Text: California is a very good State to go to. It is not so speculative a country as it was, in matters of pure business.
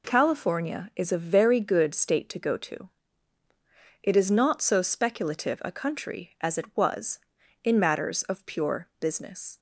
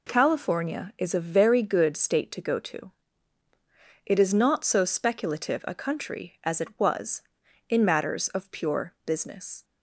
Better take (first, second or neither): neither